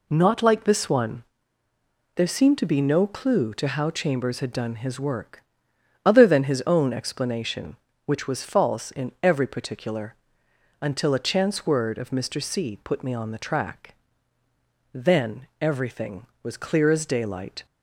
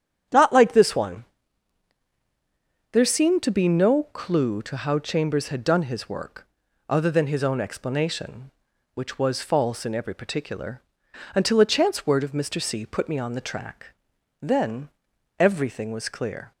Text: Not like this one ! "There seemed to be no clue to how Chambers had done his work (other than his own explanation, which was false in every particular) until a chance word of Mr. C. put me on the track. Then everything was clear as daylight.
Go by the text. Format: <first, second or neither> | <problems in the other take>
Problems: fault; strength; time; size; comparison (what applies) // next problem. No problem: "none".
first | starts louder than the rest; strong; until 2.9 s; 9 dB // pauses between "Then" and "everything"; noticeable; at 14.8 s; 0.50 s long // stops before "as daylight"; at 16.5 s